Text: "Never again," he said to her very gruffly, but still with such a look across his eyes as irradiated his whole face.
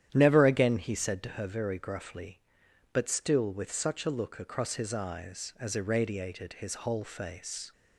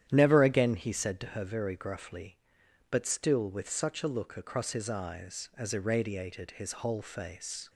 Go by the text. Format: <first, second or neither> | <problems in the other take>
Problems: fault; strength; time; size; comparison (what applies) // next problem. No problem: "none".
neither | starts louder than the rest; strong; the same in both